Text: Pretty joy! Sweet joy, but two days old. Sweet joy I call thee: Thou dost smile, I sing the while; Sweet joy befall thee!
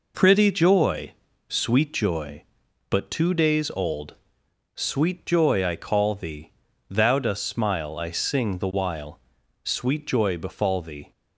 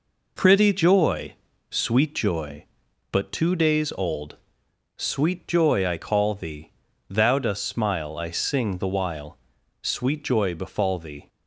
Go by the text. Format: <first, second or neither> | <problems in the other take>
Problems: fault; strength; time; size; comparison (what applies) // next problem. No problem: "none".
neither | none